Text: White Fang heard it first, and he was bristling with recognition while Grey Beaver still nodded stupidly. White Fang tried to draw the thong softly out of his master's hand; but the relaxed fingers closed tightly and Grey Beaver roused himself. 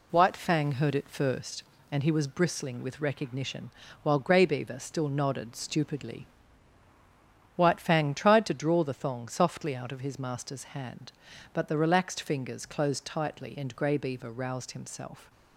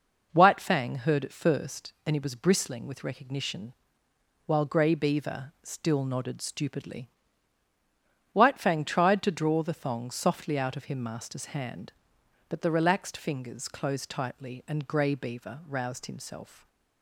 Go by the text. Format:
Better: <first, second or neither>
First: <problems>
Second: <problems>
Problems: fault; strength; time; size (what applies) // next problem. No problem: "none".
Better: first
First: pauses between "recognition" and "while"; slight; at 3.6 s; 0.32 s long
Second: pauses between "recognition" and "while"; noticeable; at 3.7 s; 0.72 s long // says "him" for "his"; at 10.8 s